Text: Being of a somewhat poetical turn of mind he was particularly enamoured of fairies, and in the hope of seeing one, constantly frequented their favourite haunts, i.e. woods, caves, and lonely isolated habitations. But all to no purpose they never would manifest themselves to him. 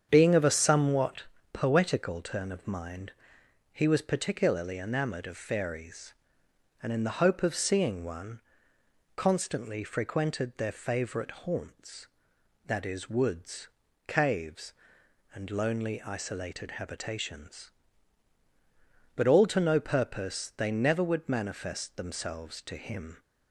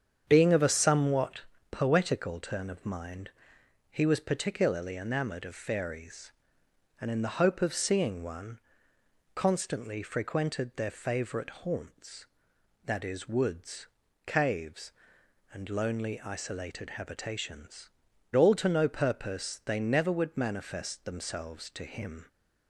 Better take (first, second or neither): first